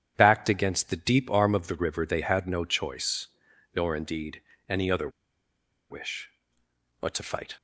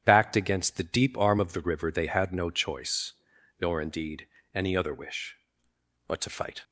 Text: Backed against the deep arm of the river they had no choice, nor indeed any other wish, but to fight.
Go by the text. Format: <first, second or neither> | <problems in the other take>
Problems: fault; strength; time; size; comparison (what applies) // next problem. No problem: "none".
second | starts louder than the rest; strong; until 1.1 s; 9 dB; strong in the second // pauses between "indeed" and "any"; slight; at 4.4 s; 0.28 s long; slight in the second // pauses between "other" and "wish"; noticeable; at 5.0 s; 0.81 s long